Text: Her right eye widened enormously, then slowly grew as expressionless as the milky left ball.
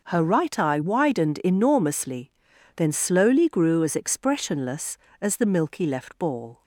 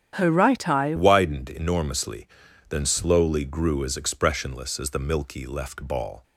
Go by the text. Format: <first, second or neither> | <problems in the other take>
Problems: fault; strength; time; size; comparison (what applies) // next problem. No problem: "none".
first | starts louder than the rest; strong; until 1.1 s; 9 dB // changes voice at "widened"; from 0.9 s on; 5.3 s long